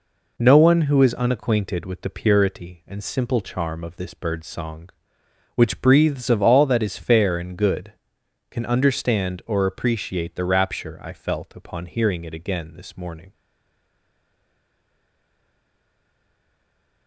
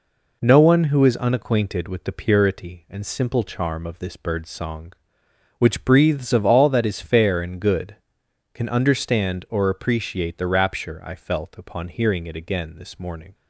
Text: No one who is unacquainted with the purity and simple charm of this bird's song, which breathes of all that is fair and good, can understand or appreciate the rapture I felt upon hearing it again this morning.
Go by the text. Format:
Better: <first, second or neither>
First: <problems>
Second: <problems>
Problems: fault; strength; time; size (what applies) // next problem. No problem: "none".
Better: second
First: stays silent after the last word; strong; from 13.3 s on; 3.7 s long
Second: none